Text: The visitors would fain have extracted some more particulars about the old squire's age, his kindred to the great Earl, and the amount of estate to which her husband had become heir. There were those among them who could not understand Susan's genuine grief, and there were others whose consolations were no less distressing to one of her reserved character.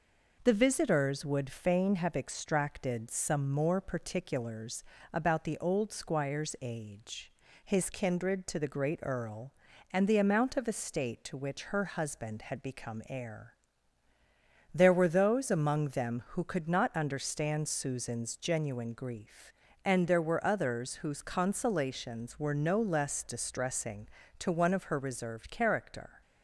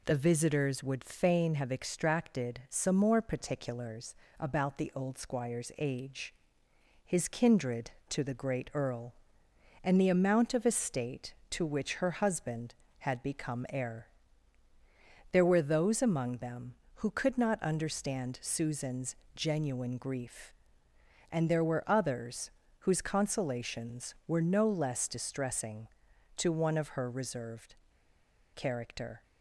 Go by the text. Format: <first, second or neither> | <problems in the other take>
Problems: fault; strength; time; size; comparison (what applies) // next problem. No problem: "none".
first | pauses between "particulars" and "about"; slight; at 4.1 s; 0.24 s long; slight in the first // pauses between "Susan's" and "genuine"; slight; at 19.1 s; 0.20 s long // pauses between "others" and "whose"; slight; at 22.4 s; 0.30 s long // pauses between "reserved" and "character"; noticeable; at 27.7 s; 0.78 s long